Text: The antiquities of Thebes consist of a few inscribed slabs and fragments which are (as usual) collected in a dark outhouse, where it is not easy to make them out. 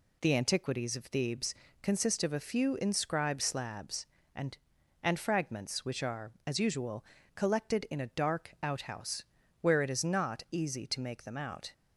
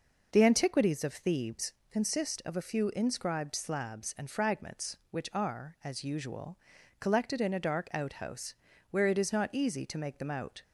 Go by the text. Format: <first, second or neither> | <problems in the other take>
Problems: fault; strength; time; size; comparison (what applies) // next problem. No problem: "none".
second | pauses between "Thebes" and "consist"; slight; at 1.5 s; 0.30 s long; slight in the second // says "and" twice; at 5.0 s